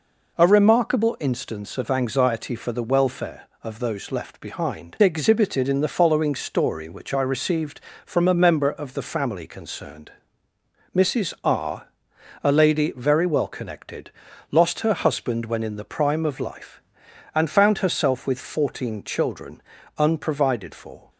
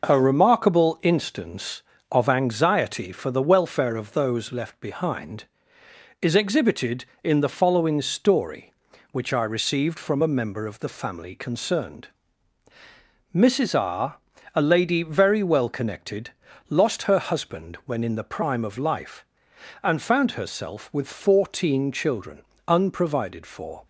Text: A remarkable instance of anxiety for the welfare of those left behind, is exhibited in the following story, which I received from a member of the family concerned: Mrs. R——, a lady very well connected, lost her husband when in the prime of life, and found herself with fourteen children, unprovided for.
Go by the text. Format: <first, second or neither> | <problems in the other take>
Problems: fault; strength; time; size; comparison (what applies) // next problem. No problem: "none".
second | skips "is"; at 4.9 s